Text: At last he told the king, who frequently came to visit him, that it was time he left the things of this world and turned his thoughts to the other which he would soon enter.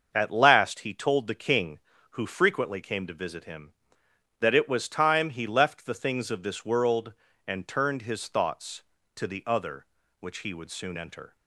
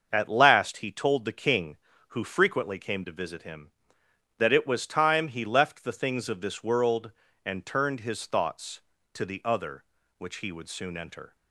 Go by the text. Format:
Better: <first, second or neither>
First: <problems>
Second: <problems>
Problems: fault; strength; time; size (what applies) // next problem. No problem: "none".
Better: neither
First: starts louder than the rest; until 1.1 s; 6.5 dB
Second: starts louder than the rest; until 1.1 s; 6.5 dB